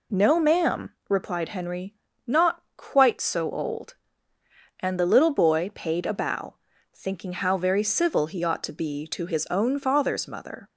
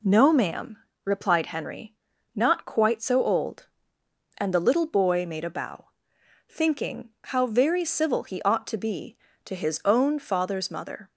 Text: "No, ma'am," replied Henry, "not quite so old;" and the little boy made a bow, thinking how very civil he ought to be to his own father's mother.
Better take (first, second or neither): second